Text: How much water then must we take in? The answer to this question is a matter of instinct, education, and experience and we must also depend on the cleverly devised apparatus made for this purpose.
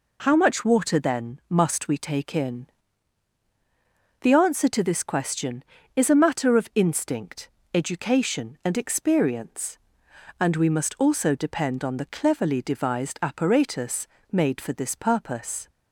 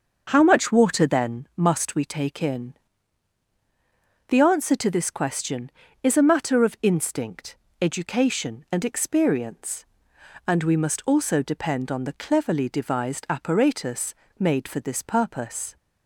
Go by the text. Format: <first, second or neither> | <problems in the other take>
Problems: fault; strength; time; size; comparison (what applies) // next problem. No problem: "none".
first | starts louder than the rest; until 1.6 s; 6.5 dB // pauses between "apparatus" and "made"; slight; at 14.1 s; 0.26 s long; slight in the first